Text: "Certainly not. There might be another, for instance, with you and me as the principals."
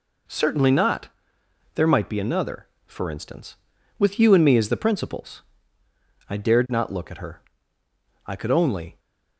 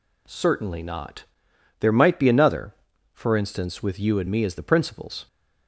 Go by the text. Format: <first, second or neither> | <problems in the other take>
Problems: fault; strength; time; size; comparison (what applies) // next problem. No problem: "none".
second | goes on to say "I dared not look at her I could only"; strong; from 6.2 s on; 2.7 s long